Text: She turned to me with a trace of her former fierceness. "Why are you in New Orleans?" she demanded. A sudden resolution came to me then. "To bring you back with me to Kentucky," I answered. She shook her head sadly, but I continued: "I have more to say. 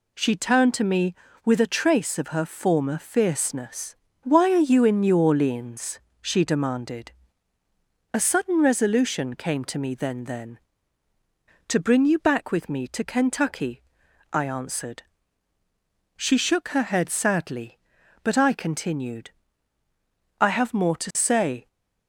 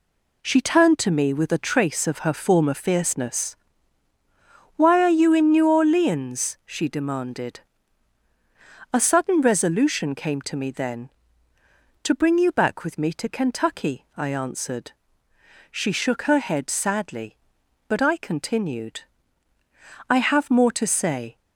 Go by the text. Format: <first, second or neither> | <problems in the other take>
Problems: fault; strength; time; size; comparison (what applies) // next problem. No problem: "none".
second | says "then" twice; at 10.2 s